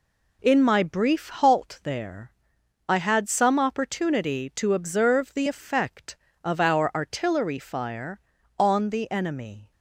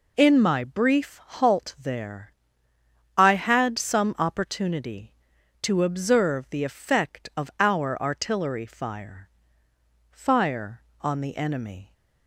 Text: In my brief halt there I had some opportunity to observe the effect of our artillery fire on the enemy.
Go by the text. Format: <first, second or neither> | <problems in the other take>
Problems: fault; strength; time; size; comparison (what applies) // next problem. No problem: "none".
first | pauses between "there" and "I"; noticeable; at 2.3 s; 0.84 s long; noticeable in the first // says "fire" twice; at 10.1 s